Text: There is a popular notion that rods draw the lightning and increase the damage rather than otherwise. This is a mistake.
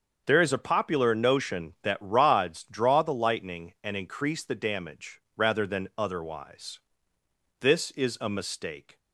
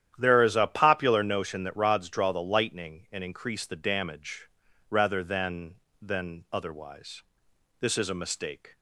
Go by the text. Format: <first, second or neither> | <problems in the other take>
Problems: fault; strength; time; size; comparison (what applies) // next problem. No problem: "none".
first | starts louder than the rest; strong; until 1.1 s; 10.5 dB; also in the first // pauses between "damage" and "rather"; at 4.4 s; 0.40 s long; slight in the first // says "than" twice; at 5.9 s